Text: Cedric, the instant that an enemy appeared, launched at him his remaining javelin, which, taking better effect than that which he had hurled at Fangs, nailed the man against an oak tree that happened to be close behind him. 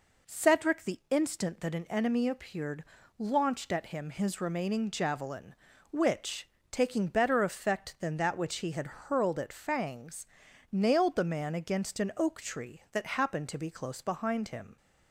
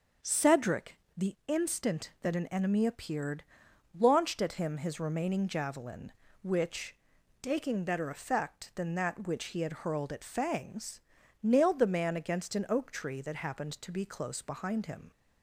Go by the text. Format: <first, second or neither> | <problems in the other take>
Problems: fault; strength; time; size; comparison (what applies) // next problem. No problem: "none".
neither | none